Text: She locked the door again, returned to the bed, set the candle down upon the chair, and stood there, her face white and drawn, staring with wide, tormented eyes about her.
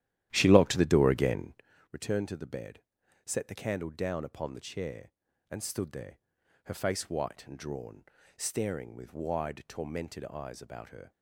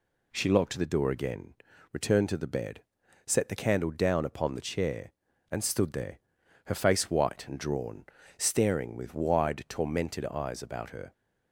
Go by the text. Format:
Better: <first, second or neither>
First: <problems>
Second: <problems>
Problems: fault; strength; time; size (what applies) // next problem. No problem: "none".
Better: second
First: starts louder than the rest; strong; until 1.7 s; 12.5 dB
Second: none